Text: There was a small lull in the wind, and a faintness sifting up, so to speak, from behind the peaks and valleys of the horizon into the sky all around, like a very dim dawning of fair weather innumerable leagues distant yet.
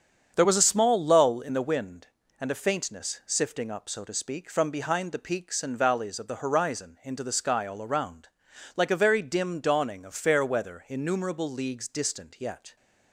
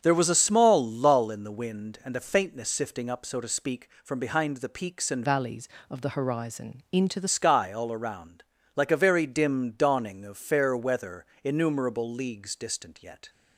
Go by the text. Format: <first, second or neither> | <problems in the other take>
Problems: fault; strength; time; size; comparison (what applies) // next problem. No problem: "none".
first | starts louder than the rest; strong; until 1.0 s; 7.5 dB; strong in the first // changes voice from "valleys" to "the"; from 5.2 to 7.2 s; 2.0 s long // pauses between "weather" and "innumerable"; slight; at 11.2 s; 0.20 s long